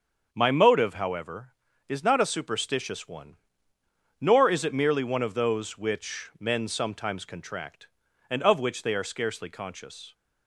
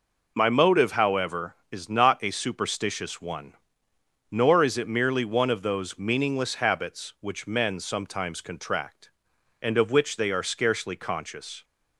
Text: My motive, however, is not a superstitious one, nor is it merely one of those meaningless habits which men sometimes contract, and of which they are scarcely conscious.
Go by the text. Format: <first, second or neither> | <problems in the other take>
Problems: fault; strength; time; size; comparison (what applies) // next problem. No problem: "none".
second | starts louder than the rest; until 1.3 s; 7 dB // skips "meaningless habits"; at 5.7 s